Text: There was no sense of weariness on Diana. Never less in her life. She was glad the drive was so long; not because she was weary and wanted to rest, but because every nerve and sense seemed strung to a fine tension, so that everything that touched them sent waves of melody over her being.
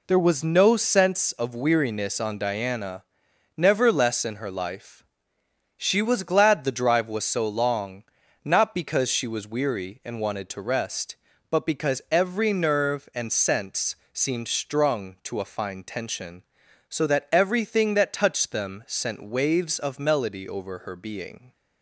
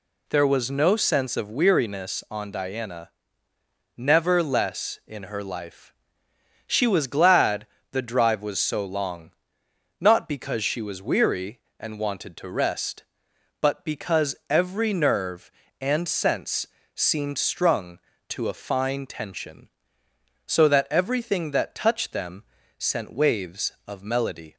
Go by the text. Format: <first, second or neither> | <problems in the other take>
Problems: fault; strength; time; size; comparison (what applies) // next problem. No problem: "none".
first | pauses between "glad" and "the"; slight; at 7.6 s; 0.24 s long // pauses between "sense" and "seemed"; slight; at 16.6 s; 0.28 s long; slight in the first // pauses between "them" and "sent"; slight; at 22.4 s; 0.34 s long // stops before "over her being"; at 24.5 s